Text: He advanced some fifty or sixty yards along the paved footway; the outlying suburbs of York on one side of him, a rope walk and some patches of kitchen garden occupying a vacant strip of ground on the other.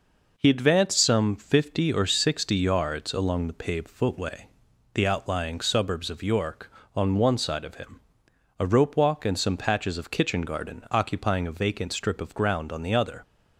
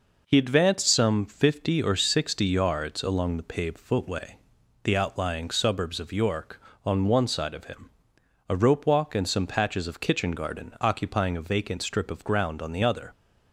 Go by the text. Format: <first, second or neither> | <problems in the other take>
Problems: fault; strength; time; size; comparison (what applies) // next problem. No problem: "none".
neither | none